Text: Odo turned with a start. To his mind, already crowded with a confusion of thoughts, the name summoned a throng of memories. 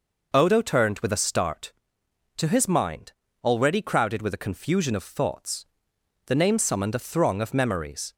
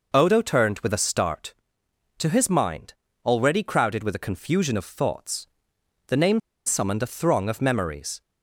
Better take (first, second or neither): first